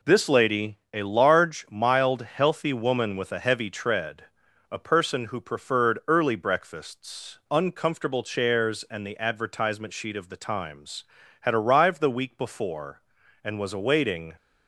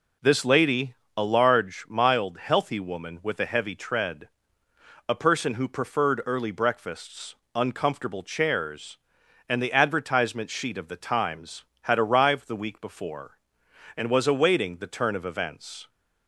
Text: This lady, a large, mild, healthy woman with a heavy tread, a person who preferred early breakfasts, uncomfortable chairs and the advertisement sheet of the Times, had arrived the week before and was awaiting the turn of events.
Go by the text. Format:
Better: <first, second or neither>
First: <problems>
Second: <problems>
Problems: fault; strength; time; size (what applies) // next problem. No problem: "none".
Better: second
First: stops before "the turn of events"; at 14.3 s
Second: none